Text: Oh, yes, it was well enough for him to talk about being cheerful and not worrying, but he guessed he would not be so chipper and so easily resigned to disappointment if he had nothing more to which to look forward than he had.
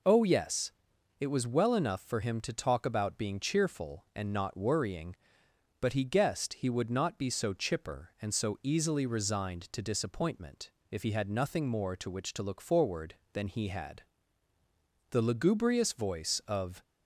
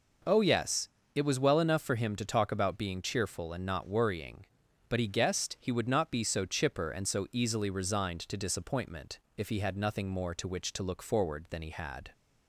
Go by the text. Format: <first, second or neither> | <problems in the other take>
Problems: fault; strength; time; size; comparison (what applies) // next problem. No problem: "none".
second | pauses between "disappointment" and "if"; slight; at 10.6 s; 0.22 s long; slight in the second // goes on to say "The lugubrious voice of"; strong; from 15.0 s on; 1.7 s long